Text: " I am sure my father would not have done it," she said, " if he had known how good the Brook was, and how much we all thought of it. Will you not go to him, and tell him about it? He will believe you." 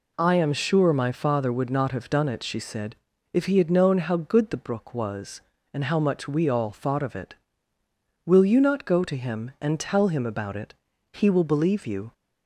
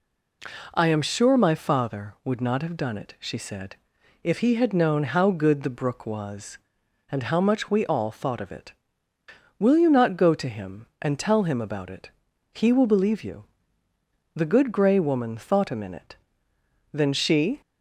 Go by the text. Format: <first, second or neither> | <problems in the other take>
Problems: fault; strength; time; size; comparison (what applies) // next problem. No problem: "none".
first | goes on to say "The Good Gray Woman thought a minute Then she"; strong; from 14.3 s on; 3.2 s long